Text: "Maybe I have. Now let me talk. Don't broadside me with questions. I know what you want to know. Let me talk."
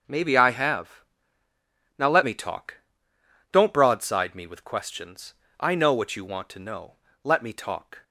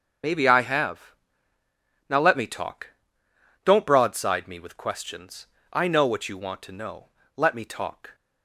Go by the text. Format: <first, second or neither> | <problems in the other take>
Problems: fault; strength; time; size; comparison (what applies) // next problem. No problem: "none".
first | loses the start of "Maybe"; at 0.2 s; 60 ms // starts louder than the rest; until 2.1 s; 6.5 dB